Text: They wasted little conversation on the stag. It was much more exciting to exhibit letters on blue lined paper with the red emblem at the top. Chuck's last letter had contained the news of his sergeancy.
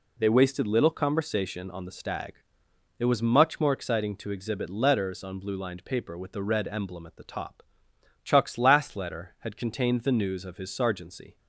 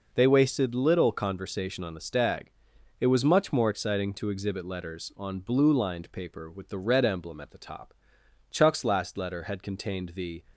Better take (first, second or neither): first